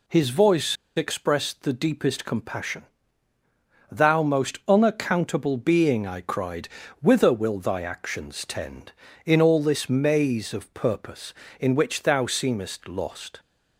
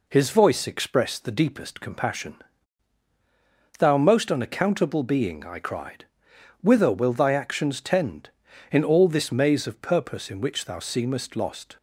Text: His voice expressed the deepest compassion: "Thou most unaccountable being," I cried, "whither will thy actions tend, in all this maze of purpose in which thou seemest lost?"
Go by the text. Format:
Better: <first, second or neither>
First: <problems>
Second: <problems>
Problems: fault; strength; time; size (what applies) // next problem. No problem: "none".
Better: second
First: pauses between "voice" and "expressed"; slight; at 0.7 s; 0.20 s long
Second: none